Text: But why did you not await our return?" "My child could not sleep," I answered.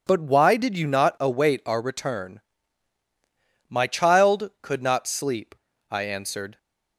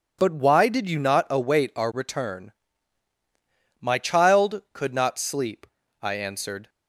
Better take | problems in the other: neither | none

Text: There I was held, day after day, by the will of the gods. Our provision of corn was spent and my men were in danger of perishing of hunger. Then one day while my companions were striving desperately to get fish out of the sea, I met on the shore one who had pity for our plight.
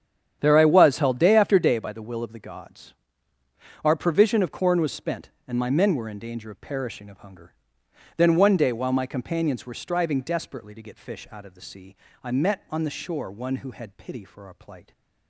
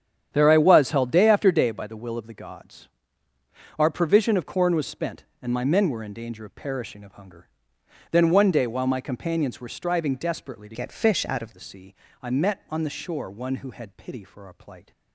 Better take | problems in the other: first | starts louder than the rest; strong; until 1.3 s; 9 dB; strong in the first // changes voice from "get" to "of"; from 10.7 to 11.5 s; 0.8 s long

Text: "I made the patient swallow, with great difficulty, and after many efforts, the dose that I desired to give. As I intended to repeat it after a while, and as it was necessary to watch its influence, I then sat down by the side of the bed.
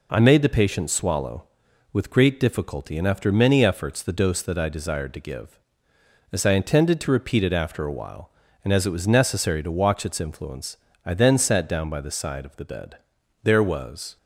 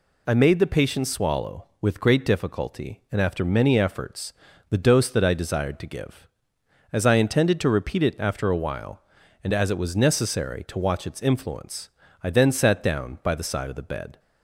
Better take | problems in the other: second | goes on to say "There was"; noticeable; from 13.4 s on; 0.74 s long

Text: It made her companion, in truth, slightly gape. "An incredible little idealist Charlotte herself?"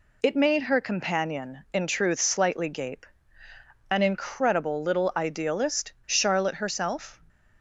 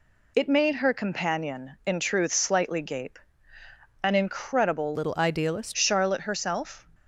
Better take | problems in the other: first | changes voice from "little" to "idealist"; from 4.9 to 5.7 s; 0.8 s long

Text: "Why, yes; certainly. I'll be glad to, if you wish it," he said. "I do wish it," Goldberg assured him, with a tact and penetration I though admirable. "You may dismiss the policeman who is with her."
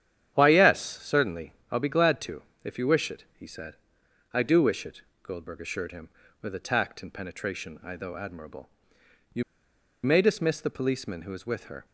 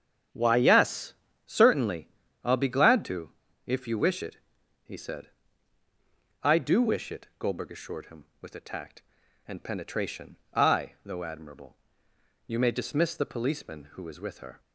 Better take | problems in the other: second | starts louder than the rest; strong; until 1.7 s; 10.5 dB; strong in the second // pauses between "You" and "may"; noticeable; at 9.4 s; 0.62 s long

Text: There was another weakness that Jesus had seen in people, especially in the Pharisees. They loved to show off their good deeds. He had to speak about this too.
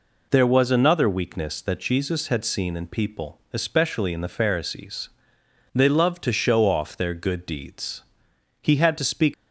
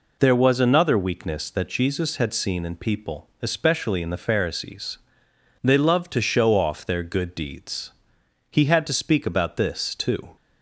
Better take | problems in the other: second | stops before "about this too"; at 9.3 s

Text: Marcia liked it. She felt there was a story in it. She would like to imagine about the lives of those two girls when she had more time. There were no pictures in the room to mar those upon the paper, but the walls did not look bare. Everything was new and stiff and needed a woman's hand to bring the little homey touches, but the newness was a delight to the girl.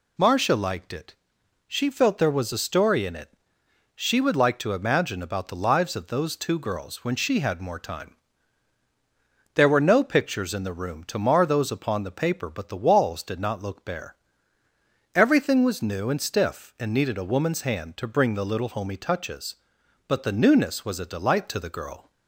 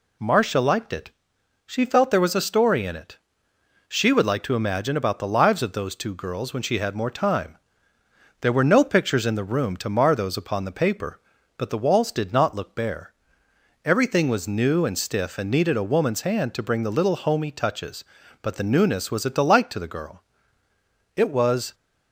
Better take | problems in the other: first | goes on to say "It was"; from 21.1 s on; 0.58 s long

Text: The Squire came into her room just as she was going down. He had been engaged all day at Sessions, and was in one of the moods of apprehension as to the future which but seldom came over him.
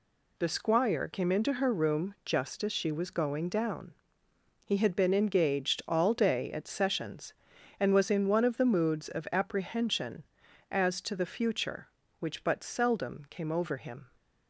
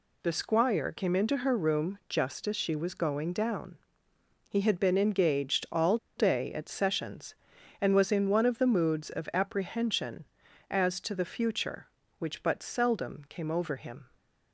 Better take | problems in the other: first | pauses between "all" and "day"; slight; at 5.9 s; 0.20 s long

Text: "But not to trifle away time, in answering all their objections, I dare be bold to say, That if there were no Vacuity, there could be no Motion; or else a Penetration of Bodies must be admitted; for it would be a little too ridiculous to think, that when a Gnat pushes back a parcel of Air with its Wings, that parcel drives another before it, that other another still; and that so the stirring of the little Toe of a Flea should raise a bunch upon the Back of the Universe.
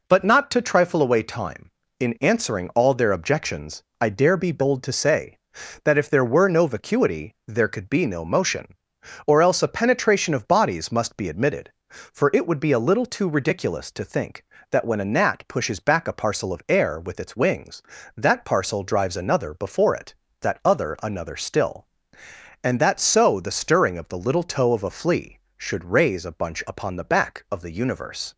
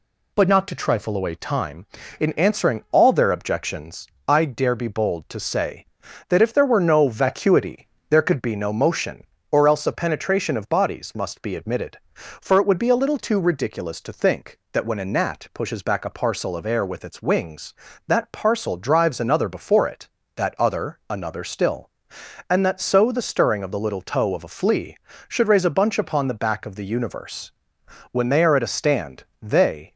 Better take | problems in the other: first | goes on to say "When they are at a stand they"; strong; from 28.1 s on; 1.8 s long

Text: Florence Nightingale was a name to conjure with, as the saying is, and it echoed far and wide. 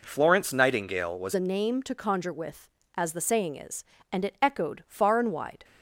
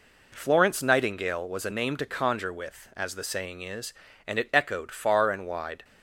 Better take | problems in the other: second | changes voice at "a"; from 1.3 s on; 4.3 s long

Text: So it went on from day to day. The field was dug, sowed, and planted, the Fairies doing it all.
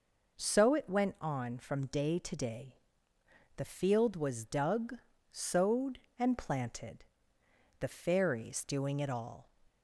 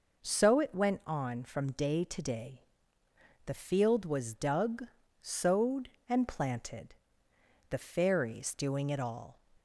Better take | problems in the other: neither | none

